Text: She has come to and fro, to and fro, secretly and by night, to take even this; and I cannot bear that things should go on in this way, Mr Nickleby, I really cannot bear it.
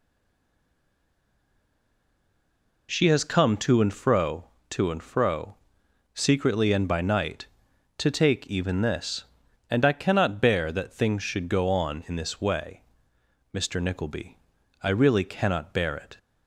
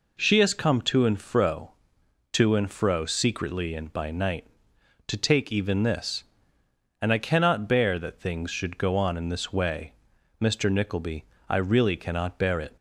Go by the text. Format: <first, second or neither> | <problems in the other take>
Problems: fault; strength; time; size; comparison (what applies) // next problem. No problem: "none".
second | stays silent before the first word; strong; until 2.8 s; 2.8 s long